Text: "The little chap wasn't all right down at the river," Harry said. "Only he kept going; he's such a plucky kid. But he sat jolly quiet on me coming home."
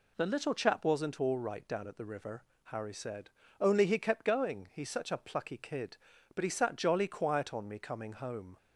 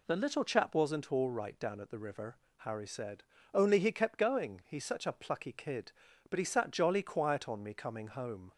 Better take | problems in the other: neither | none

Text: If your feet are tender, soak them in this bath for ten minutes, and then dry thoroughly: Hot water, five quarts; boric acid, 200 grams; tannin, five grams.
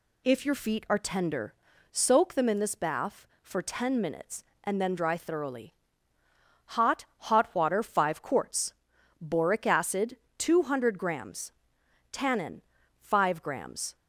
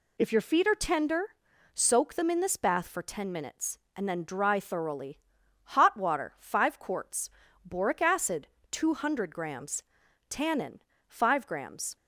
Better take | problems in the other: second | says "Hot" twice; at 7.1 s

